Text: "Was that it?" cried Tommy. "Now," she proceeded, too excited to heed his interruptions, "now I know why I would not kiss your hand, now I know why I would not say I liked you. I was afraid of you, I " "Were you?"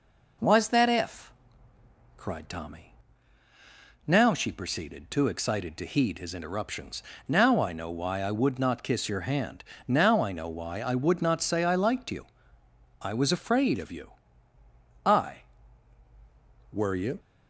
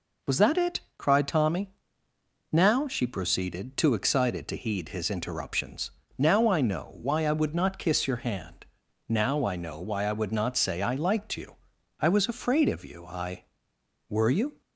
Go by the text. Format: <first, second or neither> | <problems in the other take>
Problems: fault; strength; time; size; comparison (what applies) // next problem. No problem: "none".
second | says "if" for "it"; at 0.8 s